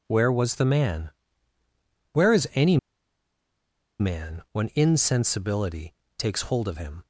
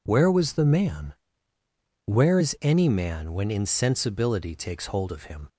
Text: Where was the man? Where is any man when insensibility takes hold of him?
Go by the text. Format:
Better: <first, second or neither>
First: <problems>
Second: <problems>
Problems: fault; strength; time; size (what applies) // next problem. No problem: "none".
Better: second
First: pauses between "any" and "man"; at 2.7 s; 1.2 s long // pauses between "insensibility" and "takes"; slight; at 5.9 s; 0.24 s long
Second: none